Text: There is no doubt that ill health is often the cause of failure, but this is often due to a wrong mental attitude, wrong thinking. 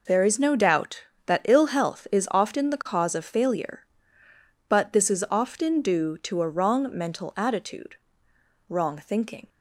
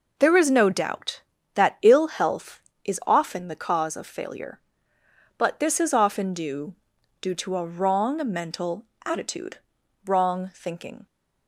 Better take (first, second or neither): first